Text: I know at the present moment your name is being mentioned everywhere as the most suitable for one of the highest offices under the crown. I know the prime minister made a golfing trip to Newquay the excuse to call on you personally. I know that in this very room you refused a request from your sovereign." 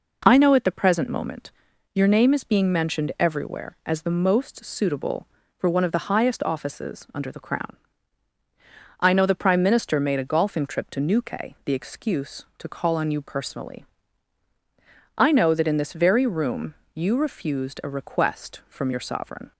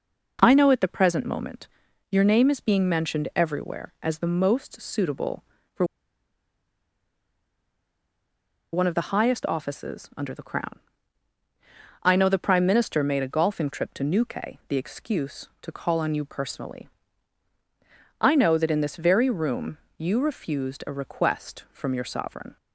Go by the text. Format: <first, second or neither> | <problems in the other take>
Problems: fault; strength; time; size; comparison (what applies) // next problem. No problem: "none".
first | pauses between "moment" and "your"; at 1.6 s; 0.42 s long; also in the first // pauses between "for" and "one"; strong; at 5.8 s; 2.8 s long // pauses between "room" and "you"; slight; at 19.7 s; 0.20 s long; slight in the first